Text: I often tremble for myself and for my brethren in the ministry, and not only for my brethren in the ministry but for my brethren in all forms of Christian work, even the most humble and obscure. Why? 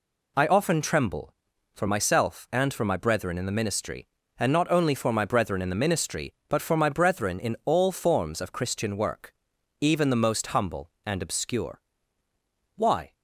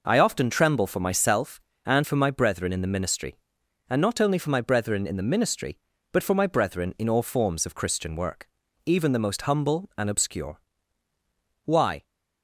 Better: neither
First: none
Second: none

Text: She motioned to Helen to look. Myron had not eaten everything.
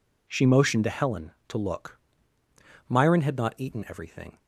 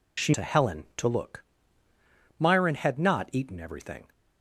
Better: first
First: none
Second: skips "motioned"; at 0.3 s

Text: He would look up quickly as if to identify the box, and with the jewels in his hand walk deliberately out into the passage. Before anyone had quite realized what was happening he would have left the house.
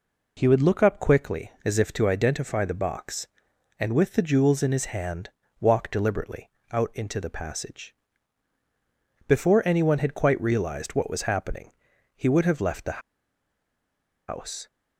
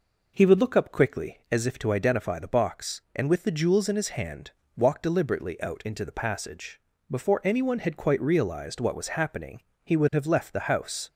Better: second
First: pauses between "hand" and "walk"; slight; at 5.2 s; 0.30 s long // pauses between "deliberately" and "out"; slight; at 6.5 s; 0.18 s long // pauses between "happening" and "he"; at 11.7 s; 0.42 s long // pauses between "the" and "house"; strong; at 13.0 s; 1.2 s long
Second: pauses between "hand" and "walk"; slight; at 4.4 s; 0.26 s long // pauses between "happening" and "he"; slight; at 9.6 s; 0.22 s long

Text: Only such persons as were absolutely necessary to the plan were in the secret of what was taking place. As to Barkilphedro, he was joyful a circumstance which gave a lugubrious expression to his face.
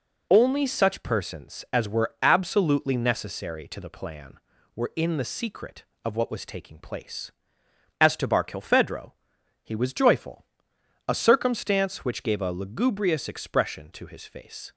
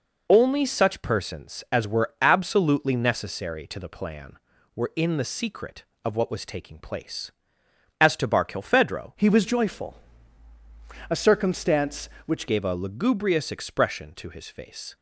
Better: first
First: pauses between "joyful" and "a"; noticeable; at 10.4 s; 0.62 s long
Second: changes voice from "he" to "which"; from 9.1 to 12.4 s; 3.3 s long // pauses between "joyful" and "a"; at 9.9 s; 1.1 s long

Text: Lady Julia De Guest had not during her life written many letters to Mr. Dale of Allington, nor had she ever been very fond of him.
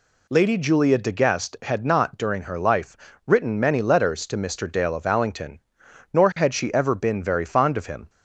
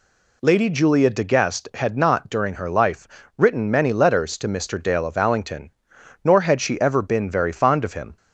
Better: neither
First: pauses between "life" and "written"; slight; at 2.9 s; 0.28 s long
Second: pauses between "life" and "written"; slight; at 3.0 s; 0.28 s long

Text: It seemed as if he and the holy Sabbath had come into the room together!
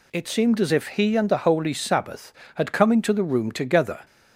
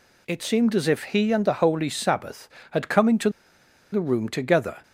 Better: first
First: none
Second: pauses between "into" and "the"; noticeable; at 3.2 s; 0.63 s long

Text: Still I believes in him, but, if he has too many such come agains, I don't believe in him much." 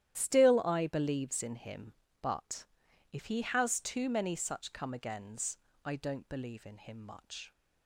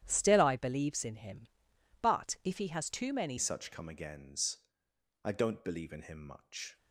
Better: first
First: starts louder than the rest; strong; until 1.1 s; 11.5 dB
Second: starts louder than the rest; strong; until 1.0 s; 10.5 dB // changes voice at "such"; from 3.3 s on; 3.4 s long

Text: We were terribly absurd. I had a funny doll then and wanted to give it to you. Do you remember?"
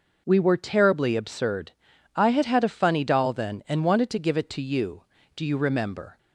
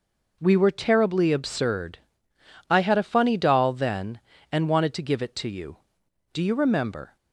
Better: second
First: says "had" twice; at 2.4 s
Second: none

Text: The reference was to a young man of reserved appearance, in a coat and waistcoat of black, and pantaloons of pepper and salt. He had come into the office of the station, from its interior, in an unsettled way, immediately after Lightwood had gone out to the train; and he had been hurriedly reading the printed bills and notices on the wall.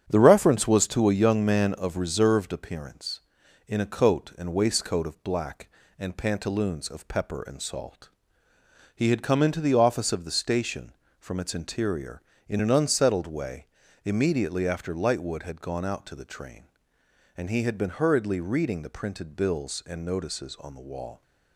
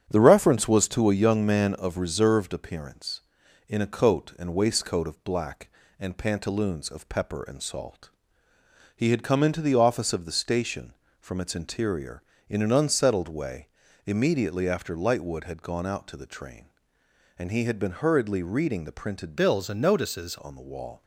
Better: first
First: starts louder than the rest; strong; until 1.0 s; 9.5 dB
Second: starts louder than the rest; strong; until 1.1 s; 9 dB // changes voice from "bills" to "notices"; from 19.3 to 20.3 s; 1.0 s long

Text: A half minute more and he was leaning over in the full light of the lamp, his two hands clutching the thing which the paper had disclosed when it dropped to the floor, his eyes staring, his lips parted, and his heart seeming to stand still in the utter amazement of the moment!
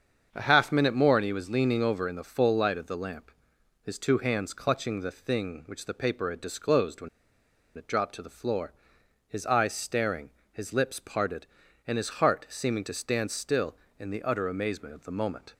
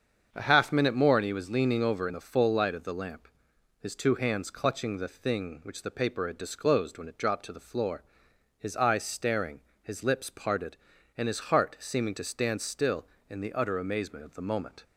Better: second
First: starts louder than the rest; until 1.3 s; 7 dB // pauses between "when" and "it"; noticeable; at 7.0 s; 0.67 s long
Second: starts louder than the rest; until 1.3 s; 7 dB

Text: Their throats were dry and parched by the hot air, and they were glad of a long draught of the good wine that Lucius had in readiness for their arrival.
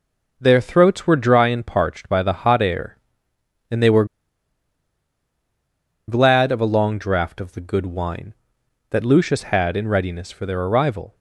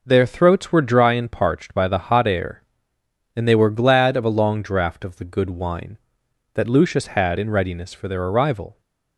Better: second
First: pauses between "were" and "glad"; strong; at 4.0 s; 2.0 s long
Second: none

